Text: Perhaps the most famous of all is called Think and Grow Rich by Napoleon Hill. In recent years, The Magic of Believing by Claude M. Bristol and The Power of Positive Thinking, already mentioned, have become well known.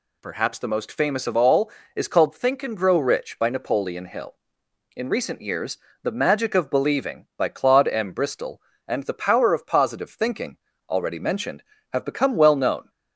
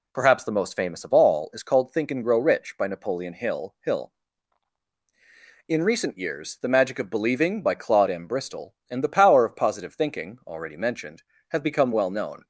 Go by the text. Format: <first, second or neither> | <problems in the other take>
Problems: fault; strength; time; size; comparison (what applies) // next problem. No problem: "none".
first | says "Hill" twice; at 3.8 s